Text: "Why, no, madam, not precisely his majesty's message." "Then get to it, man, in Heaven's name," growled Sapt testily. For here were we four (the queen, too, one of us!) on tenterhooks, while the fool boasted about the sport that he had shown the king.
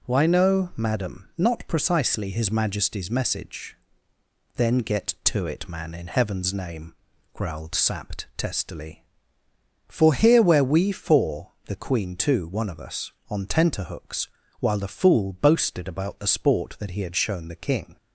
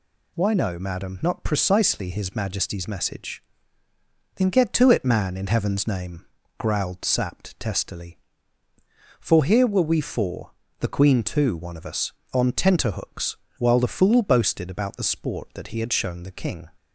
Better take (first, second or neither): second